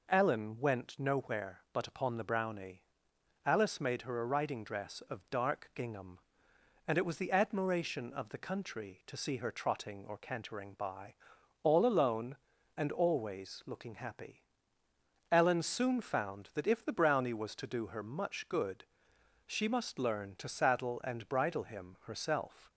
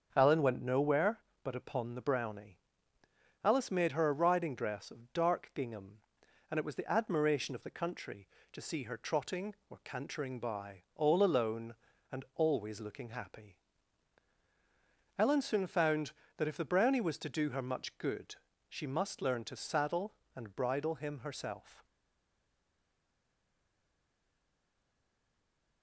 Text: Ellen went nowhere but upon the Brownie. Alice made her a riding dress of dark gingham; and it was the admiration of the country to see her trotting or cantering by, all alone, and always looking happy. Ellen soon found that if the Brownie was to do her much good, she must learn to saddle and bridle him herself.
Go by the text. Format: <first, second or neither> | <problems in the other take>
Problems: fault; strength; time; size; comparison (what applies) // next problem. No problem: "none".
first | starts louder than the rest; until 1.1 s; 7 dB // stays silent after the last word; strong; from 21.8 s on; 4.0 s long